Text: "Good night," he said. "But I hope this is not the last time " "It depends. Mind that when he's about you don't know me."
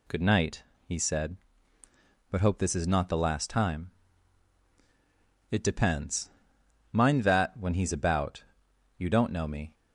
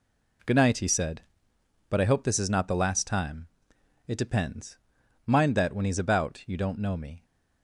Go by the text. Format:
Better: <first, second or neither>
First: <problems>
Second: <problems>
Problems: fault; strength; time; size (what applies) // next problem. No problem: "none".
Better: second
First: skips "I"; at 2.3 s // pauses between "about" and "you"; noticeable; at 8.4 s; 0.52 s long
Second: none